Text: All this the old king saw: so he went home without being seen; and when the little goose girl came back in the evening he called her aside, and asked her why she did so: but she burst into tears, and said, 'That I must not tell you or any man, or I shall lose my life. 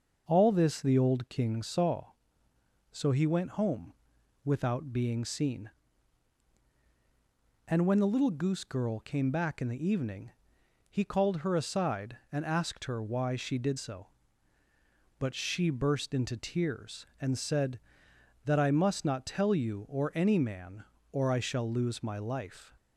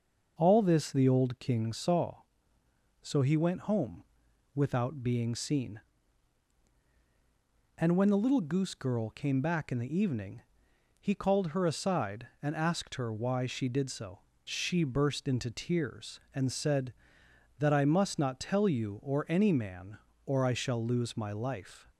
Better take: first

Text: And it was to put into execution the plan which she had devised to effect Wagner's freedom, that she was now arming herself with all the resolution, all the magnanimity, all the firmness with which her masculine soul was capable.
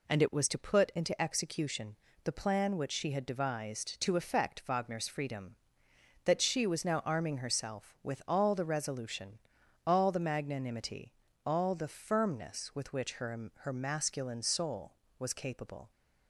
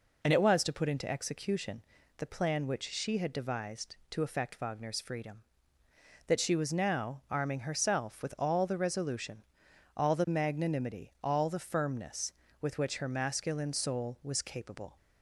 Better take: second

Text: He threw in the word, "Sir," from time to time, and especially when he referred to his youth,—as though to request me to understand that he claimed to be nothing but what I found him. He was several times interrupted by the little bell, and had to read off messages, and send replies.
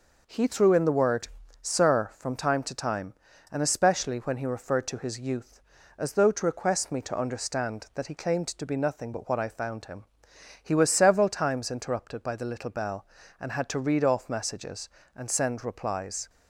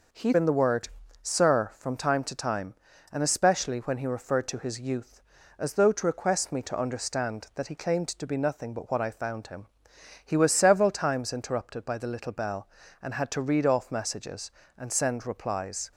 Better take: first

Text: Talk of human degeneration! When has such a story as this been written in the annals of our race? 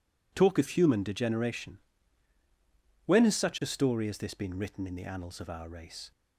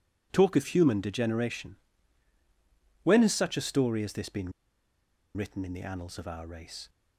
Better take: first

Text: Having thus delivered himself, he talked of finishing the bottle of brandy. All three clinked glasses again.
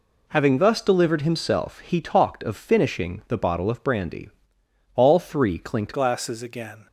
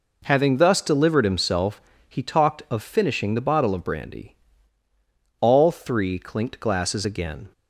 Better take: second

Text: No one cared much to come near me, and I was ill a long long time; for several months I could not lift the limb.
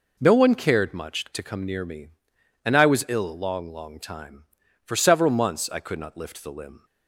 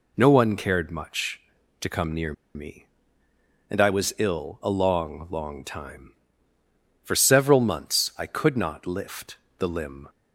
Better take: first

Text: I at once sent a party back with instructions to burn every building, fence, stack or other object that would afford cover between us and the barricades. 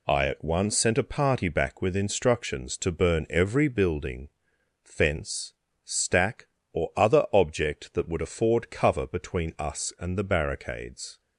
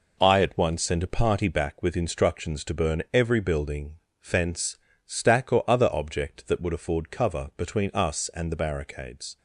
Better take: neither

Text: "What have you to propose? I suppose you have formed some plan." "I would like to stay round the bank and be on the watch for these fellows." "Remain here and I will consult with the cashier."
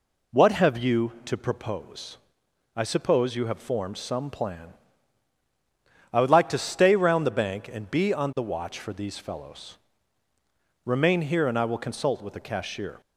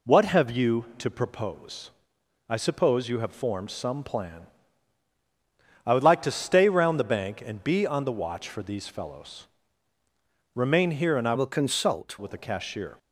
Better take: first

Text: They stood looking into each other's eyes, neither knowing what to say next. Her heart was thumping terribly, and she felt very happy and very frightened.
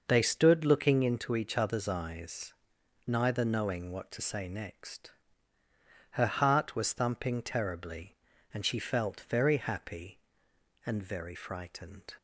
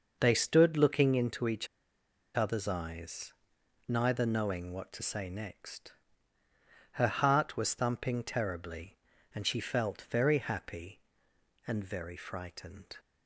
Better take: first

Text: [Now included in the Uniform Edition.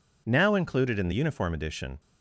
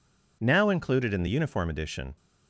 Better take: neither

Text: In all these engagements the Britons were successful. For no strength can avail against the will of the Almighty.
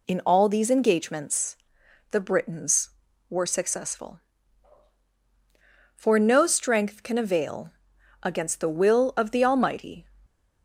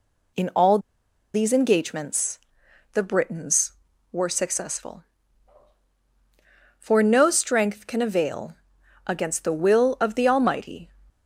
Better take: first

